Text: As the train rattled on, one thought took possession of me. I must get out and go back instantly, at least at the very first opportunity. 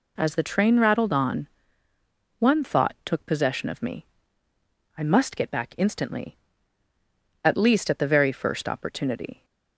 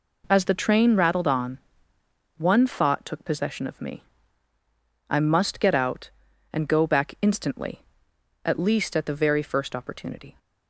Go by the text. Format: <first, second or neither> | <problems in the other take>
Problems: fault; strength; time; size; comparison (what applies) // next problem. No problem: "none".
second | skips "out and go"; at 5.5 s